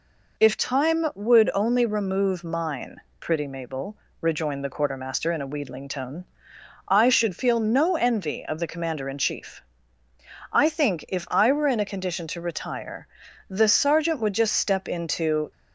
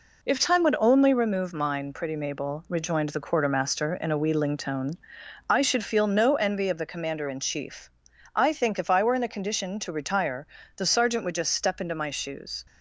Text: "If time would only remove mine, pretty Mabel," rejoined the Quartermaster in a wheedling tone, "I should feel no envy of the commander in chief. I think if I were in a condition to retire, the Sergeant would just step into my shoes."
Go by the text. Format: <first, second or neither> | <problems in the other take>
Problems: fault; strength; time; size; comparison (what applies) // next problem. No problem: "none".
second | stops before "my shoes"; at 15.5 s